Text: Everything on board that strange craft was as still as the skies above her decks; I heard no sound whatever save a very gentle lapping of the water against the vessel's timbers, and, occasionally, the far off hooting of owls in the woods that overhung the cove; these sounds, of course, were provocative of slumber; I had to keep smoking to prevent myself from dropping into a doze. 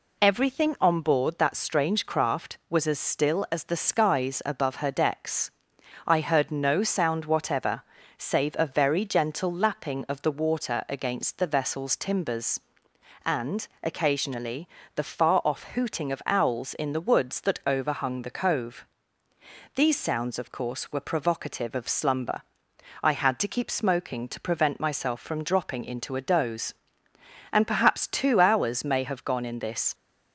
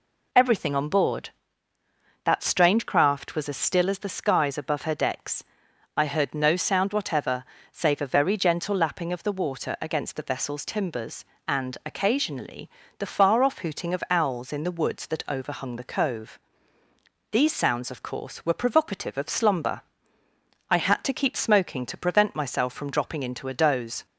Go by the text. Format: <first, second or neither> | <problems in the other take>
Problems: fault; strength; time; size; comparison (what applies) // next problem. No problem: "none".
second | pauses between "whatever" and "save"; slight; at 7.8 s; 0.34 s long; slight in the second // goes on to say "And perhaps two hours may have gone in this"; strong; from 27.5 s on; 2.4 s long